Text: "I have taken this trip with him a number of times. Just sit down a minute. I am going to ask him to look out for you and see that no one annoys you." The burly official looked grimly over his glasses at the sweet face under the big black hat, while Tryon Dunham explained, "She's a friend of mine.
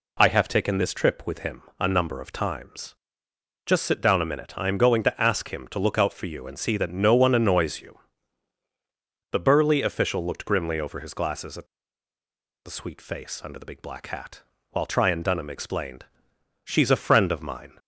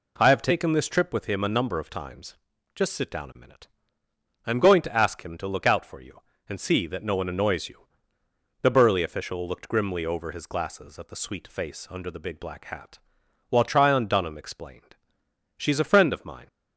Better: second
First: pauses between "him" and "a"; slight; at 1.6 s; 0.16 s long // pauses between "at" and "the"; at 11.6 s; 0.98 s long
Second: none

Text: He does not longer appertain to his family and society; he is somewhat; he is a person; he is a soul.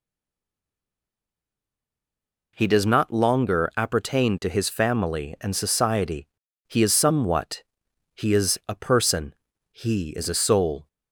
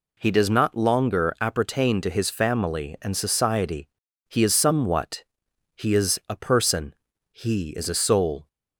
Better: second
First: stays silent before the first word; strong; until 2.5 s; 2.5 s long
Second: none

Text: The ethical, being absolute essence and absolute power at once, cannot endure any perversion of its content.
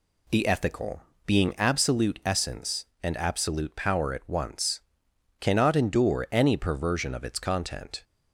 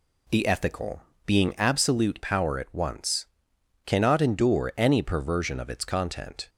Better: first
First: none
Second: skips "essence and absolute"; at 2.2 s

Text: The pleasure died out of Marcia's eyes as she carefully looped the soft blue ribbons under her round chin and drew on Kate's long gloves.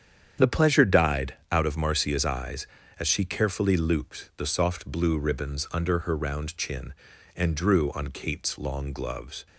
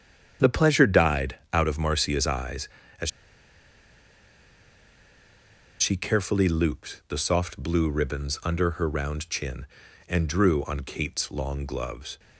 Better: first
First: starts louder than the rest; strong; until 1.5 s; 8.5 dB // pauses between "died" and "out"; slight; at 1.3 s; 0.18 s long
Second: starts louder than the rest; strong; until 1.5 s; 8.5 dB // pauses between "died" and "out"; slight; at 1.3 s; 0.18 s long // pauses between "as" and "she"; strong; at 3.1 s; 2.7 s long

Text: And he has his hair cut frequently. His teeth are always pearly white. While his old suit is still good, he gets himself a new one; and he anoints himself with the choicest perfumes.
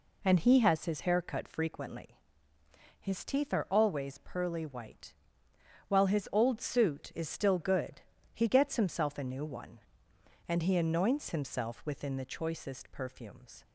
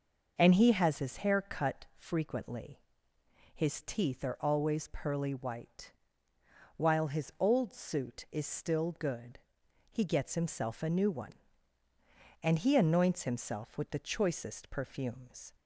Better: second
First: says "within" for "with"; at 11.8 s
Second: none

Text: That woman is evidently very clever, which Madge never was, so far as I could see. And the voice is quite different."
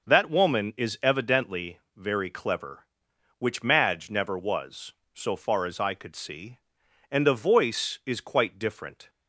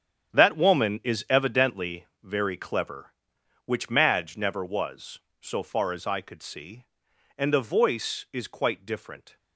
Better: first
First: pauses between "evidently" and "very"; slight; at 1.7 s; 0.16 s long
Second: gets quieter; strong; throughout; 10.5 dB // pauses between "evidently" and "very"; slight; at 2.0 s; 0.16 s long

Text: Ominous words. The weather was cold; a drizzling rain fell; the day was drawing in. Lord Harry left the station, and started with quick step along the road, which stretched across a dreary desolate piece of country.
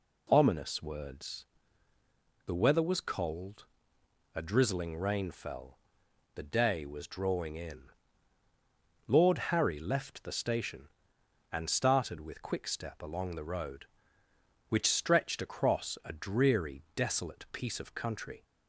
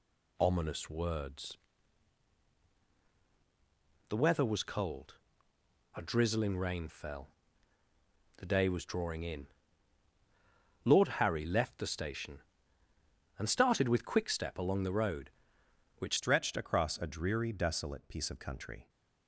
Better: first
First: none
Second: changes voice at "stretched"; from 16.1 s on; 2.7 s long

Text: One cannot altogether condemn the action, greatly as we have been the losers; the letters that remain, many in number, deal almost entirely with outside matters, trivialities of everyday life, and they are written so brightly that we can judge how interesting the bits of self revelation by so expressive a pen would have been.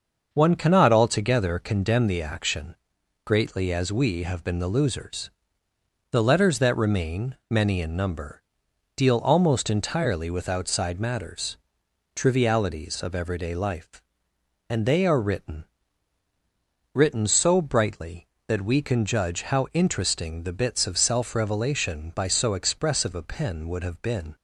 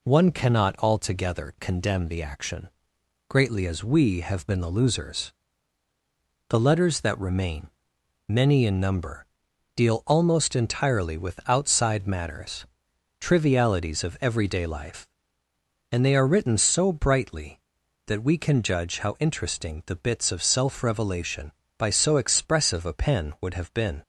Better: second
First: starts louder than the rest; until 1.3 s; 6.5 dB // says "written" twice; at 16.9 s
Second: none

